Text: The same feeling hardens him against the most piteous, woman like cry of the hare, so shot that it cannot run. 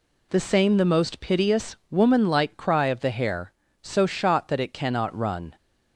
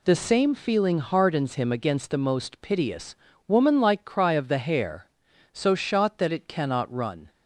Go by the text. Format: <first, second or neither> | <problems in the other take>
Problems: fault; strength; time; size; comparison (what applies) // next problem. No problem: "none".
second | skips "feeling hardens him against"; at 0.7 s